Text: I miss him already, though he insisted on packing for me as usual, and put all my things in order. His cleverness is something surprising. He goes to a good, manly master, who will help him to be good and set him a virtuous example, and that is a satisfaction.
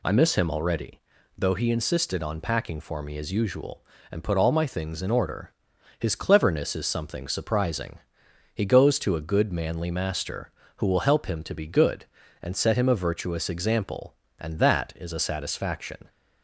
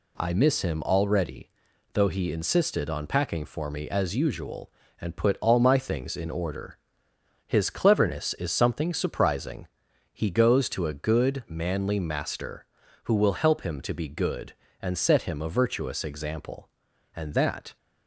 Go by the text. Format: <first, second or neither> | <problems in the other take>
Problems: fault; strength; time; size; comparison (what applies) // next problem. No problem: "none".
first | stops before "is a satisfaction"; at 17.7 s